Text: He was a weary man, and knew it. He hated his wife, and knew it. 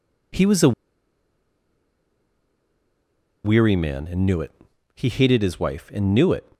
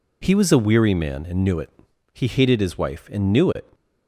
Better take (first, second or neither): second